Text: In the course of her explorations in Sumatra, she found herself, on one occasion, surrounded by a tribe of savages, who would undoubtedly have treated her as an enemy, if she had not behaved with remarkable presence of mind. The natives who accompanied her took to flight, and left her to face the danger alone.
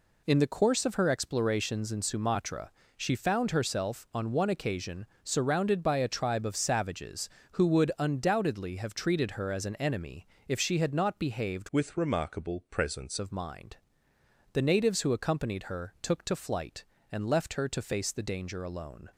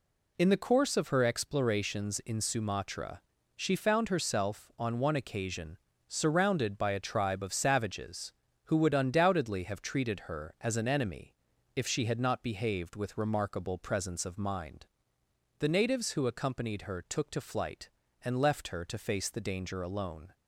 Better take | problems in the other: second | changes voice from "with" to "presence"; from 11.7 to 13.1 s; 1.4 s long

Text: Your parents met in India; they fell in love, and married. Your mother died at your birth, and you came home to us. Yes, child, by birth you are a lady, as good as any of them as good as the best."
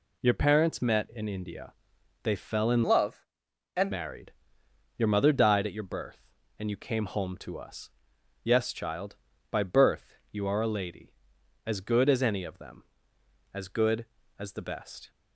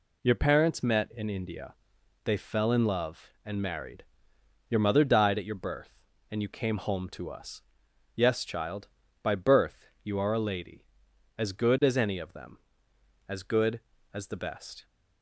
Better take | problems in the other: second | changes voice from "love" to "and"; from 2.8 to 3.9 s; 1.1 s long // pauses between "birth" and "you"; slight; at 10.1 s; 0.18 s long; slight in the second

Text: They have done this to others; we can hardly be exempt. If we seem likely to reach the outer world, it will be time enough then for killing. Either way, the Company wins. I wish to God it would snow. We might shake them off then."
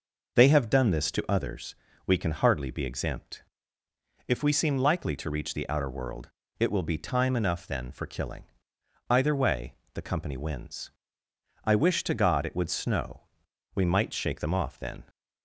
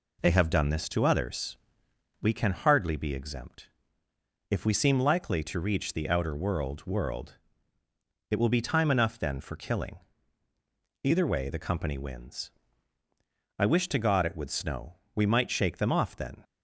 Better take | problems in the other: first | says "world" twice; at 6.8 s

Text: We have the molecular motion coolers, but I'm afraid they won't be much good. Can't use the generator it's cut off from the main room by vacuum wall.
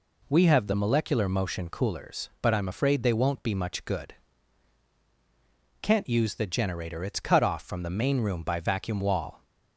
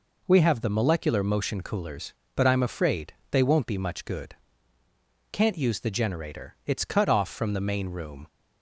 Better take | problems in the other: first | pauses between "afraid" and "they"; slight; at 3.1 s; 0.18 s long // stops before "by vacuum wall"; at 8.2 s

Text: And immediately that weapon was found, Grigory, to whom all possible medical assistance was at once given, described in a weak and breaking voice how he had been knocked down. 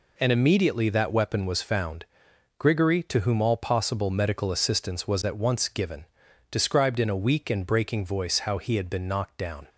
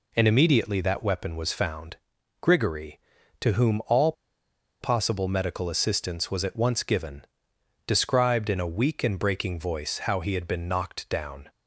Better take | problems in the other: first | pauses between "all" and "possible"; noticeable; at 4.1 s; 0.68 s long

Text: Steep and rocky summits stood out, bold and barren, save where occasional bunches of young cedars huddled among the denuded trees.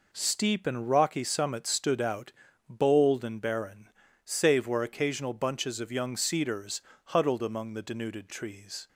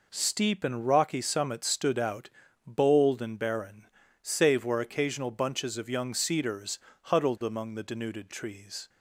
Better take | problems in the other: neither | pauses between "cedars" and "huddled"; slight; the same in both

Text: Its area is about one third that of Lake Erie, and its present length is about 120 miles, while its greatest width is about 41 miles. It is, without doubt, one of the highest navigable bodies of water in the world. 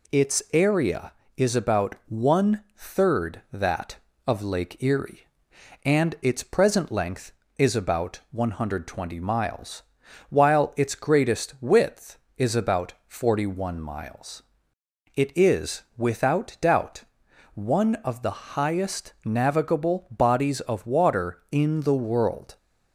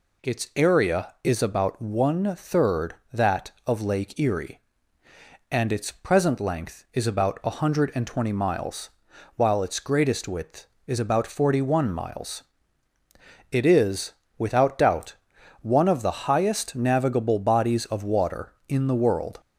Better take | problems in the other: neither | none

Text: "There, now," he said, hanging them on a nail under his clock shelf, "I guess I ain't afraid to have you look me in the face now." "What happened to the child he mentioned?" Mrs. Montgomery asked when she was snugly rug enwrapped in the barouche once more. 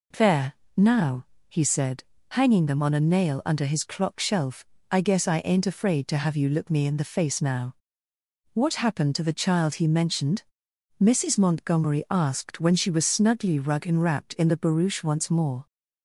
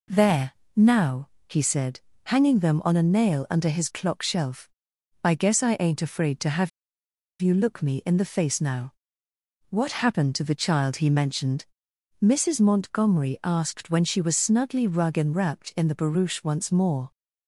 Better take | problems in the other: first | pauses between "have" and "you"; noticeable; at 6.6 s; 0.72 s long

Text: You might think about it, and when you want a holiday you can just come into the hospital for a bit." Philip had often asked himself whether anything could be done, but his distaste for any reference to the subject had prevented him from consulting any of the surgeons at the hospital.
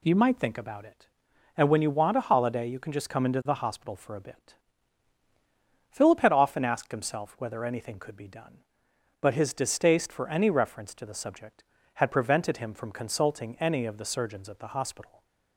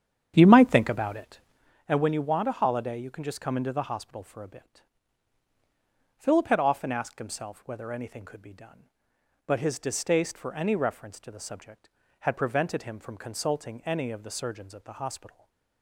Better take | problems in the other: first | starts louder than the rest; strong; until 1.8 s; 9 dB // stays silent after the last word; slight; from 15.2 s on; 0.6 s long

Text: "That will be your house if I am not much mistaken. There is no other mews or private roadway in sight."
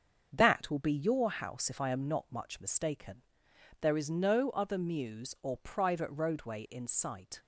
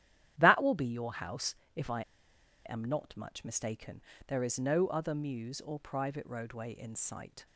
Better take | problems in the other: first | starts louder than the rest; strong; until 1.3 s; 11.5 dB; strong in the first // pauses between "house" and "if"; slight; at 1.5 s; 0.20 s long // pauses between "I" and "am"; noticeable; at 2.0 s; 0.63 s long

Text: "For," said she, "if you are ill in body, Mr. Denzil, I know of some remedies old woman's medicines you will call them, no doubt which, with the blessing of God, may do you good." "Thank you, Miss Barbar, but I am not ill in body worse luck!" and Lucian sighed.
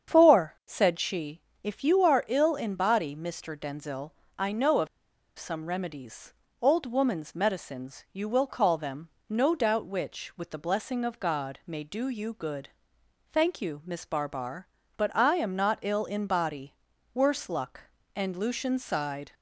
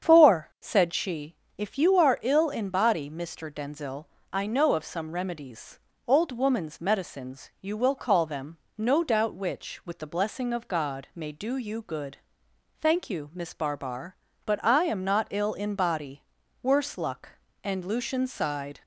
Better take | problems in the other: second | starts louder than the rest; strong; until 1.1 s; 7.5 dB; strong in the second // pauses between "of" and "some"; noticeable; at 4.8 s; 0.49 s long // pauses between "remedies" and "old"; slight; at 6.3 s; 0.28 s long; slight in the second // pauses between "body" and "worse"; at 16.7 s; 0.40 s long; also in the second

